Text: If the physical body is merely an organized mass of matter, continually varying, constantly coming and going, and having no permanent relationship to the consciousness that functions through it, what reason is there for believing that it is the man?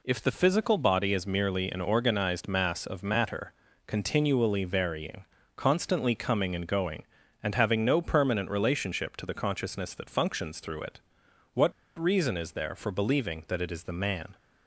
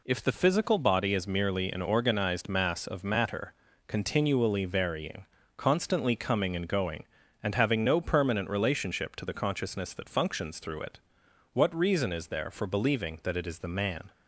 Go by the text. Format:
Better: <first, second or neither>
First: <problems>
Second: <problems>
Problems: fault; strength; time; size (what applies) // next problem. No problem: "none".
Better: second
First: pauses between "what" and "reason"; slight; at 11.7 s; 0.25 s long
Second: none